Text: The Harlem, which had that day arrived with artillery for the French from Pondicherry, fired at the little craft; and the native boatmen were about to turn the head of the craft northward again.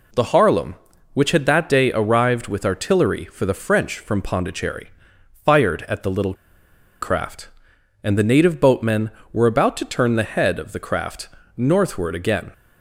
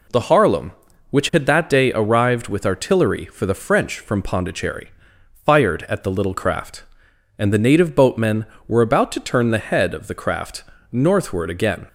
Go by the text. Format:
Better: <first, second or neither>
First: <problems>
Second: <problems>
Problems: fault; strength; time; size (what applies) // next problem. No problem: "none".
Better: second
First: pauses between "little" and "craft"; noticeable; at 6.3 s; 0.68 s long // pauses between "craft" and "northward"; slight; at 11.2 s; 0.28 s long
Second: pauses between "craft" and "northward"; slight; at 10.6 s; 0.28 s long